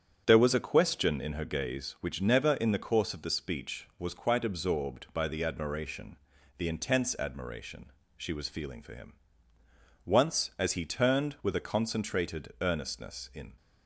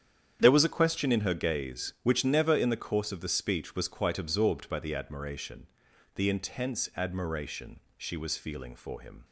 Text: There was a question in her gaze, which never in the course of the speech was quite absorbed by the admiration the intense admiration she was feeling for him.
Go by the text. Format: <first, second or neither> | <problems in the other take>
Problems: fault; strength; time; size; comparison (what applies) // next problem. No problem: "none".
second | starts louder than the rest; strong; until 1.2 s; 8.5 dB; strong in the second // pauses between "admiration" and "the"; at 6.1 s; 0.40 s long; noticeable in the second // pauses between "admiration" and "she"; slight; at 7.9 s; 0.26 s long; slight in the second // goes on to say "Once as he turned with a concentrated earnestness in"; strong; from 10.0 s on; 3.4 s long